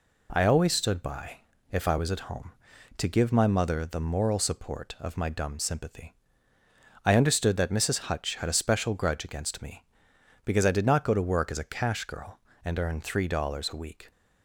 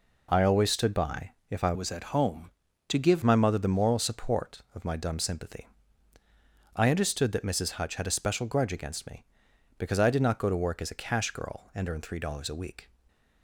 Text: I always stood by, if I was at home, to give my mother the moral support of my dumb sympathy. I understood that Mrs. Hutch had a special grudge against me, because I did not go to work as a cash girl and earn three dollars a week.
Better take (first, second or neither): first